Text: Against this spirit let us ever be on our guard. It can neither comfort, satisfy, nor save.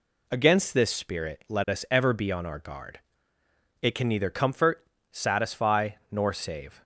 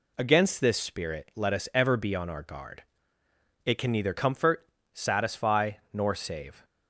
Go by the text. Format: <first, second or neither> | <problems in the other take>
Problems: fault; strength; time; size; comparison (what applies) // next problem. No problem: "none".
neither | none